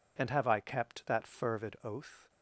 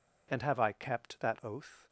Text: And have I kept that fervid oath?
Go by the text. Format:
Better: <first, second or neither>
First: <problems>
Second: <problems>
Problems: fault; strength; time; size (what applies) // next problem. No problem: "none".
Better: first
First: none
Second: skips "fervid"; at 1.4 s